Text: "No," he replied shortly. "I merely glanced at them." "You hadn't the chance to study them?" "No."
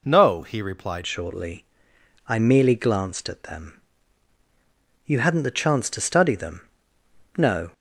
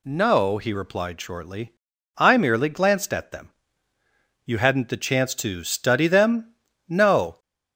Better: second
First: changes voice at "shortly"; from 1.0 s on; 6.7 s long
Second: none

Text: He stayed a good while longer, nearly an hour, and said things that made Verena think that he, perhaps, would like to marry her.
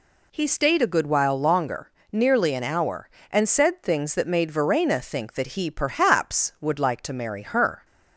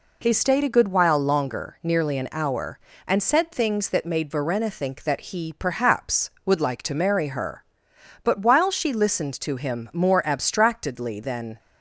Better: first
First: none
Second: goes on to say "But while she listened to him more abstractedly than"; strong; from 8.2 s on; 3.3 s long

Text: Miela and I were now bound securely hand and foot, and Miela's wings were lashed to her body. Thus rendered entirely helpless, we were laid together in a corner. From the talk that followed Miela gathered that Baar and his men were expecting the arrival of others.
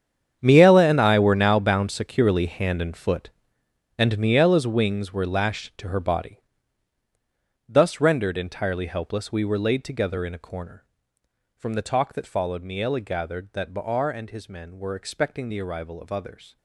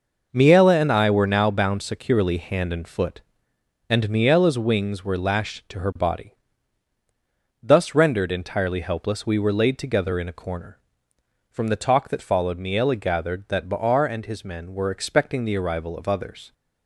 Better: second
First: gets quieter; strong; throughout; 15.5 dB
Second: none

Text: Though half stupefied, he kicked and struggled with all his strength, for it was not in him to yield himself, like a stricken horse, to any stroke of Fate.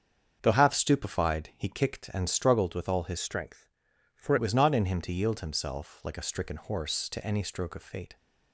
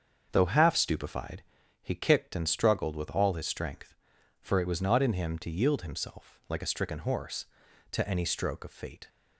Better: second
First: starts louder than the rest; strong; until 1.4 s; 7 dB // changes voice from "strength" to "for"; from 3.1 to 4.3 s; 1.2 s long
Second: starts louder than the rest; until 1.3 s; 7 dB

